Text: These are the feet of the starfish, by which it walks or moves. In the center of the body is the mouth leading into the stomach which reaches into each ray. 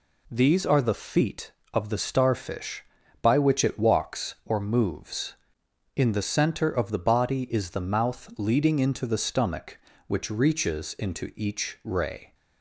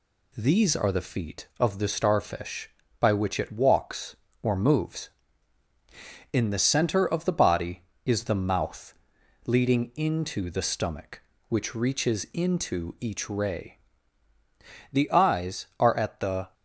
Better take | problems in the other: first | pauses between "mouth" and "leading"; noticeable; at 8.9 s; 0.50 s long // goes on to say "The eyes are at the"; from 14.9 s on; 1.6 s long

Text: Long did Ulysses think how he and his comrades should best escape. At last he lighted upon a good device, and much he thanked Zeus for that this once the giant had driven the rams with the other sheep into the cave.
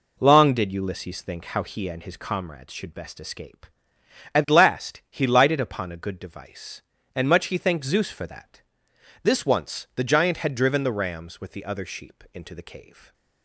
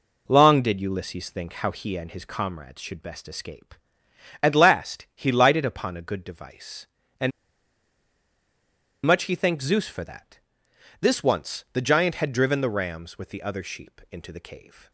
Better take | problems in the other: first | pauses between "and" and "much"; strong; at 7.3 s; 1.7 s long // pauses between "that" and "this"; noticeable; at 10.3 s; 0.62 s long; noticeable in the first

